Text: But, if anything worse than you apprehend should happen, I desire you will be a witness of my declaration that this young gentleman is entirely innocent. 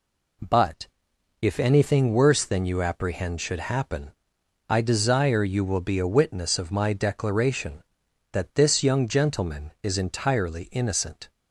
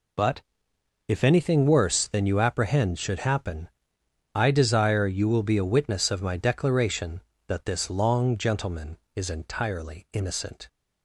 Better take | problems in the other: first | says "long" for "young"; at 7.8 s

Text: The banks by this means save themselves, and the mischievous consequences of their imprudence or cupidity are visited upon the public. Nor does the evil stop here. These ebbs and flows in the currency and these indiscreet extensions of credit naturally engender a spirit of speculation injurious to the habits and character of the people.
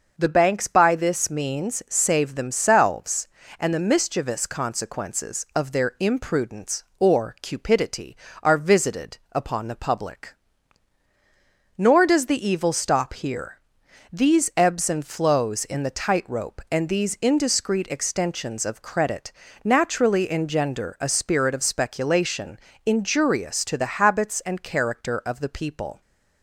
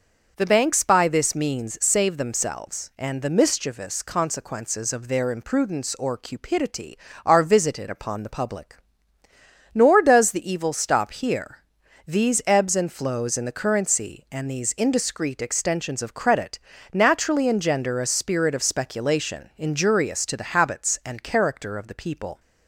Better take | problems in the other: second | starts louder than the rest; noticeable; until 1.2 s; 6 dB; noticeable in the second // says "tightrope" for "currency"; at 15.9 s // pauses between "credit" and "naturally"; slight; at 19.3 s; 0.32 s long; slight in the second // pauses between "speculation" and "injurious"; slight; at 22.5 s; 0.28 s long

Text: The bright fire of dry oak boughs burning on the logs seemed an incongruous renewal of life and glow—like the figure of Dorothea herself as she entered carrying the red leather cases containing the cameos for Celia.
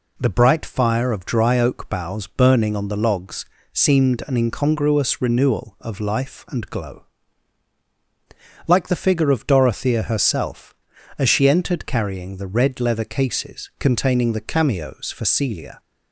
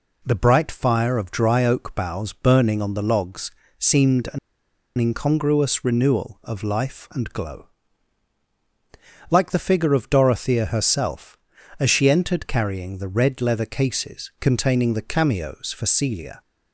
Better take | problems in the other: first | pauses between "logs" and "seemed"; slight; at 3.5 s; 0.26 s long; slight in the first // pauses between "an" and "incongruous"; noticeable; at 4.3 s; 0.59 s long

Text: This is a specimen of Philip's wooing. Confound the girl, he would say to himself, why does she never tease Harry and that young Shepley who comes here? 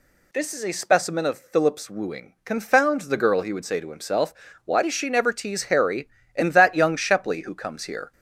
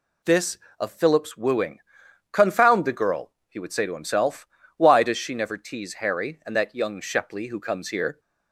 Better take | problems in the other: first | skips "is a specimen"; at 0.6 s

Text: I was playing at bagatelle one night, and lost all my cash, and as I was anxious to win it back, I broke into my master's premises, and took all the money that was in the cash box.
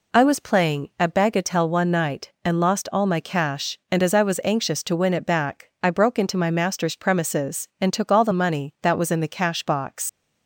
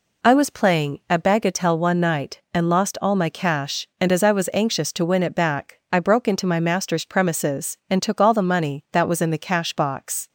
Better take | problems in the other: second | leaves "box" unfinished; at 10.0 s; 85 ms

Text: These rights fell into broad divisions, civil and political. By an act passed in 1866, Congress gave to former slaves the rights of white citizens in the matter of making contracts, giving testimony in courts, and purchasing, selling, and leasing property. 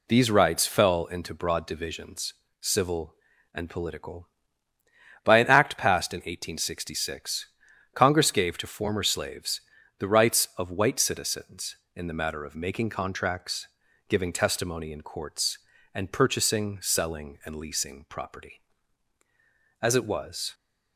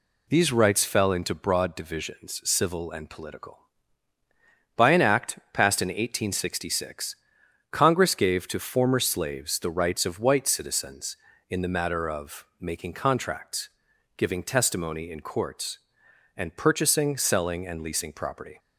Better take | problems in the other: second | pauses between "slaves" and "the"; at 9.6 s; 0.38 s long // goes on to say "As it was"; noticeable; from 19.7 s on; 0.74 s long

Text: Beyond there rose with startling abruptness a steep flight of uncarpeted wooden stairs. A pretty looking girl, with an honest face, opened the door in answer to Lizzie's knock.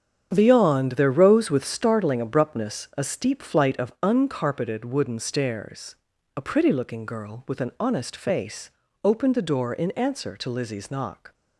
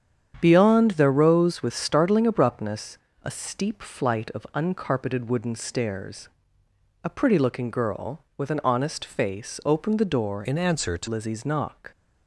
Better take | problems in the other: first | starts louder than the rest; strong; until 1.4 s; 8.5 dB; strong in the first // pauses between "abruptness" and "a"; slight; at 2.9 s; 0.26 s long // changes voice from "in" to "to"; from 10.4 to 11.0 s; 0.6 s long

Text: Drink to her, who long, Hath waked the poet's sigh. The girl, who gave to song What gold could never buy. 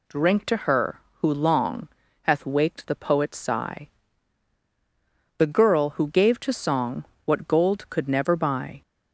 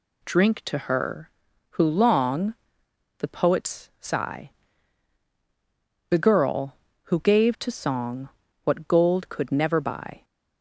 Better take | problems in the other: first | skips "Hath waked"; at 2.8 s // pauses between "song" and "What"; slight; at 8.2 s; 0.36 s long; slight in the first

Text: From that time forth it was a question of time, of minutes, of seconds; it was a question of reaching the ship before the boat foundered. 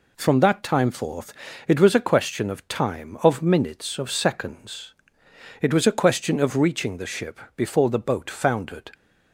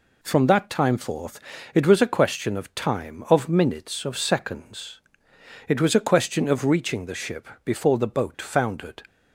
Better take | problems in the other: neither | pauses between "forth" and "it"; slight; the same in both // pauses between "ship" and "before"; slight; the same in both

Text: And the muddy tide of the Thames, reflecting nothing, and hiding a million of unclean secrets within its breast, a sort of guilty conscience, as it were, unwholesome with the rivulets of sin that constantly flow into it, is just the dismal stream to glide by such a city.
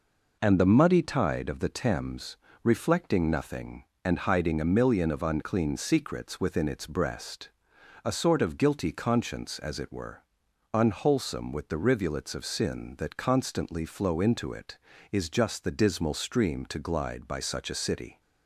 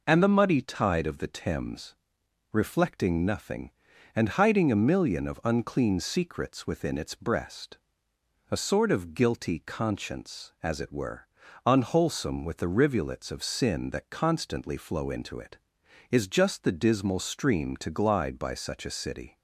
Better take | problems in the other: neither | none

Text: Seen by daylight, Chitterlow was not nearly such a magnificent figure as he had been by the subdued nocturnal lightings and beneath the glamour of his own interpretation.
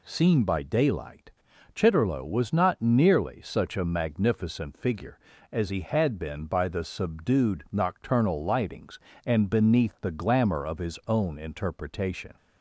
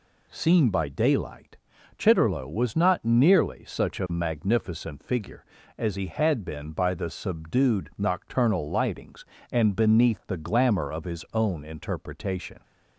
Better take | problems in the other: neither | none

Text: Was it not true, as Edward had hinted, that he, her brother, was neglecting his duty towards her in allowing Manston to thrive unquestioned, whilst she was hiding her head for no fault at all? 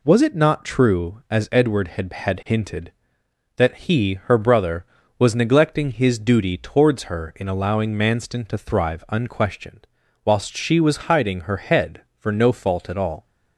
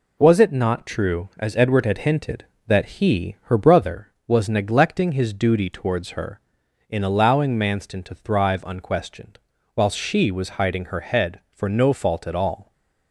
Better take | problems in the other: second | says "had" twice; at 2.1 s

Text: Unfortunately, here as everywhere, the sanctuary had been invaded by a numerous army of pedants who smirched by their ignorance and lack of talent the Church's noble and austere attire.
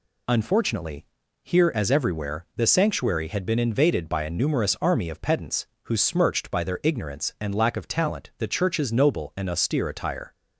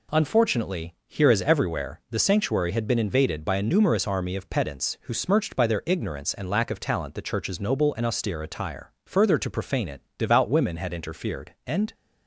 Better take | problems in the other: first | goes on to say "Further to profane it devout women had interfered and"; strong; from 9.0 s on; 2.8 s long

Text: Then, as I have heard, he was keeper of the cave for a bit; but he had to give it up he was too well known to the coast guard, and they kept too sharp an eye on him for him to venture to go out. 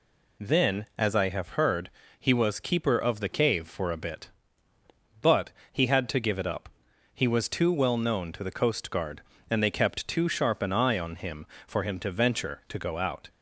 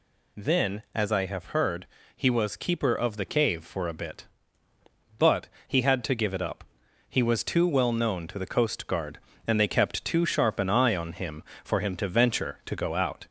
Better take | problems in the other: first | gets louder; slight; throughout; 2.5 dB // pauses between "but" and "he"; slight; at 5.4 s; 0.18 s long; slight in the first // pauses between "up" and "he"; noticeable; at 6.6 s; 0.48 s long; noticeable in the first

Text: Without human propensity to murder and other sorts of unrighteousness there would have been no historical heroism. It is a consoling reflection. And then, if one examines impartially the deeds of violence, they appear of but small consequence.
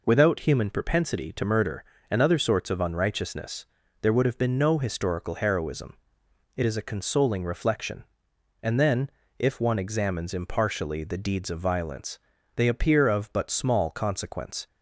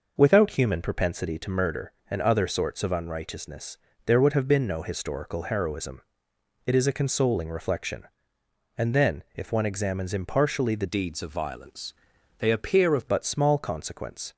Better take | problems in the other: first | pauses between "unrighteousness" and "there"; slight; at 3.7 s; 0.30 s long; slight in the first // changes voice from "deeds" to "of"; from 10.8 to 13.0 s; 2.2 s long

